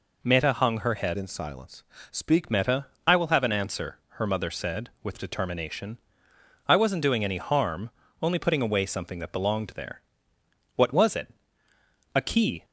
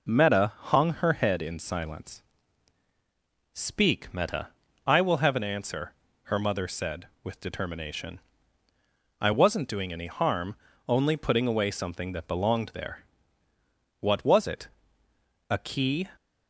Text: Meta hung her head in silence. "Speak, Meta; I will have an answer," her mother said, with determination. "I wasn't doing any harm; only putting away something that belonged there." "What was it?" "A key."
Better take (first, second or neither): second